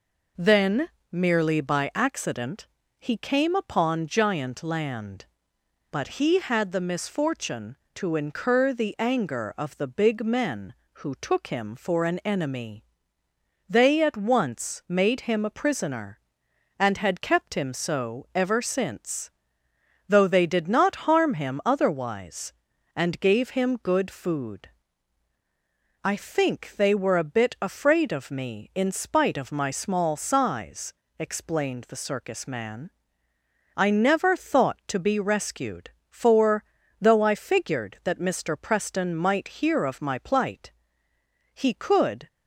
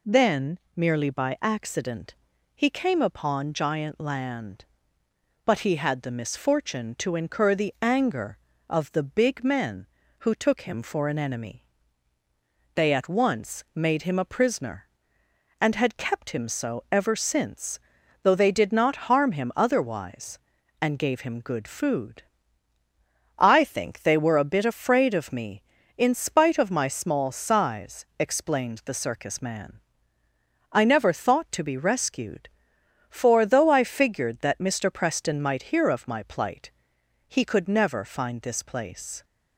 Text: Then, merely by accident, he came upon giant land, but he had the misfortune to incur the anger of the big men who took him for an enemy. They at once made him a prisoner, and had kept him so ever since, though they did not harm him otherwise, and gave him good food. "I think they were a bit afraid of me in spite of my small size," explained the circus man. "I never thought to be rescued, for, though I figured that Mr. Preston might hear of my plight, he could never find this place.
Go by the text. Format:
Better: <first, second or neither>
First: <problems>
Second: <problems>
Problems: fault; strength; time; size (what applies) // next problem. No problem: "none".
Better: second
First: stops before "never find this place"; at 42.2 s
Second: none